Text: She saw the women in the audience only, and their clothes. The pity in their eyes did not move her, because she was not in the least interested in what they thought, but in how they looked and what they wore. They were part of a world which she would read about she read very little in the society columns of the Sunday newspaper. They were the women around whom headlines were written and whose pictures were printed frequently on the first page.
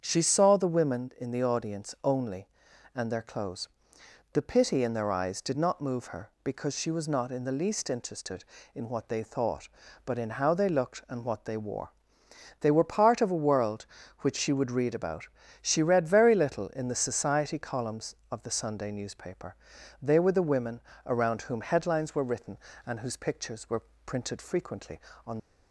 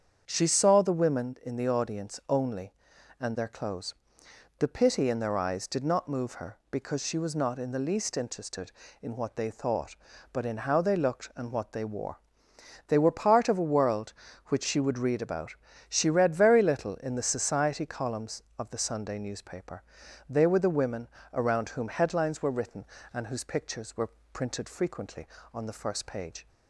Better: second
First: starts louder than the rest; strong; until 1.0 s; 7.5 dB // pauses between "about" and "she"; slight; at 15.2 s; 0.34 s long // pauses between "women" and "around"; slight; at 20.7 s; 0.26 s long // pauses between "were" and "printed"; slight; at 23.8 s; 0.22 s long // stops before "the first page"; at 25.3 s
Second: starts louder than the rest; strong; until 1.2 s; 7.5 dB // pauses between "about" and "she"; slight; at 15.5 s; 0.34 s long // pauses between "women" and "around"; slight; at 21.0 s; 0.26 s long // pauses between "were" and "printed"; slight; at 24.0 s; 0.22 s long

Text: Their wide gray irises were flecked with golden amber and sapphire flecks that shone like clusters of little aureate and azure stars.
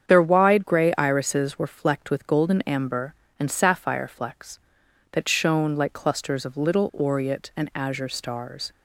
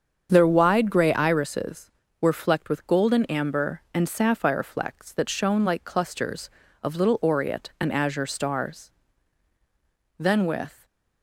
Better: first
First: starts louder than the rest; strong; until 1.1 s; 8 dB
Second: starts louder than the rest; strong; until 1.3 s; 7 dB // goes on to say "Then with"; noticeable; from 10.1 s on; 0.66 s long // stays silent after the last word; slight; from 10.7 s on; 0.5 s long

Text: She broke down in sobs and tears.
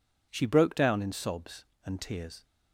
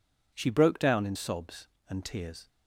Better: neither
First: none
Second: none

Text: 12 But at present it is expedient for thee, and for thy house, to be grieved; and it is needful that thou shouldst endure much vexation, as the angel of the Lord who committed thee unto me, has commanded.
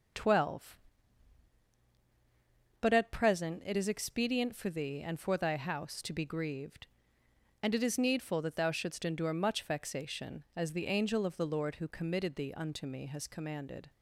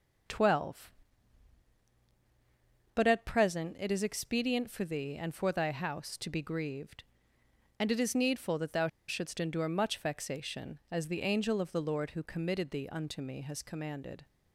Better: first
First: none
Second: pauses between "thou" and "shouldst"; slight; at 8.8 s; 0.20 s long

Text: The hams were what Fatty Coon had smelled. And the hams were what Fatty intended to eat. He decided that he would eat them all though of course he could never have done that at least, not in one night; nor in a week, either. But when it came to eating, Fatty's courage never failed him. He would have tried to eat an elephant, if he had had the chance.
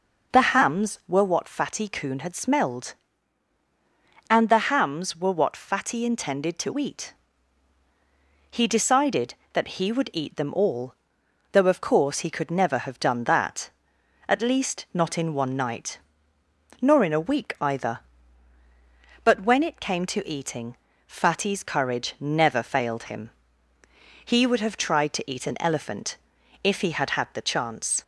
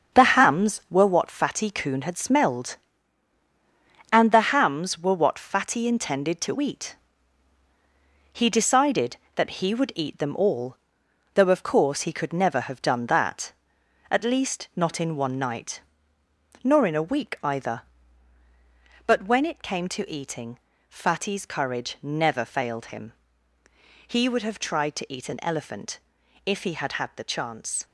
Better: first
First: pauses between "all" and "though"; noticeable; at 10.9 s; 0.60 s long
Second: gets quieter; strong; throughout; 7.5 dB // pauses between "all" and "though"; noticeable; at 10.7 s; 0.60 s long

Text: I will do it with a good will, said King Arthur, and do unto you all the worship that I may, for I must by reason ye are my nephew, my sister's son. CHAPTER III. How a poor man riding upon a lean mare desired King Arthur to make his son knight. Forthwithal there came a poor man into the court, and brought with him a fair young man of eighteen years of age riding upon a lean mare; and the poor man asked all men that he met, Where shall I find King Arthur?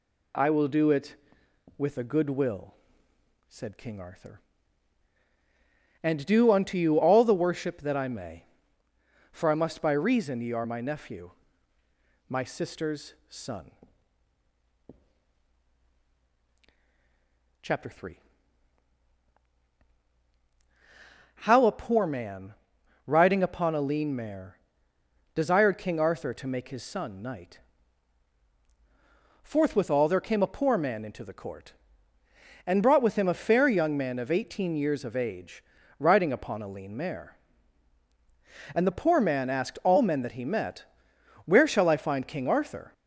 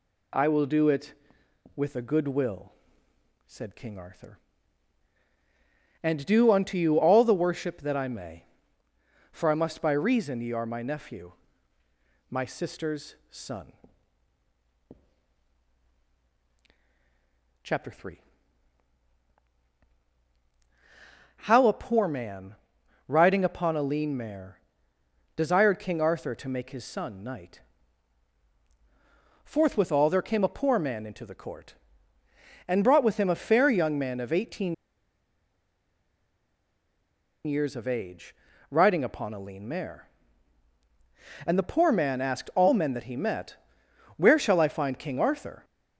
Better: first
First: pauses between "sister's" and "son"; slight; at 13.1 s; 0.16 s long // pauses between "man" and "riding"; noticeable; at 22.5 s; 0.50 s long // pauses between "mare" and "desired"; noticeable; at 24.5 s; 0.78 s long // pauses between "age" and "riding"; slight; at 35.6 s; 0.36 s long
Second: pauses between "sister's" and "son"; slight; at 13.1 s; 0.16 s long // pauses between "man" and "riding"; noticeable; at 22.5 s; 0.50 s long // pauses between "mare" and "desired"; noticeable; at 24.5 s; 0.78 s long // pauses between "eighteen" and "years"; strong; at 34.7 s; 2.7 s long // pauses between "age" and "riding"; slight; at 38.3 s; 0.36 s long

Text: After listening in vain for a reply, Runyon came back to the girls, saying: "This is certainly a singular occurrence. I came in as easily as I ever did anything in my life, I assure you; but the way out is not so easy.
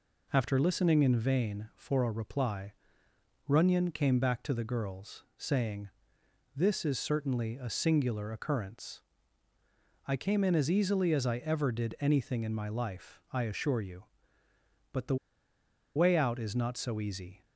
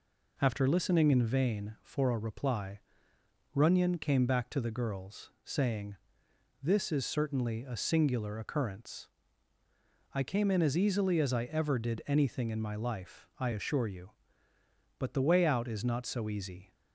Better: second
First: pauses between "the" and "way"; noticeable; at 15.1 s; 0.80 s long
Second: none

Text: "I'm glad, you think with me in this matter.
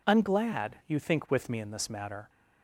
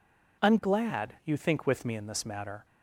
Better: neither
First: none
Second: none

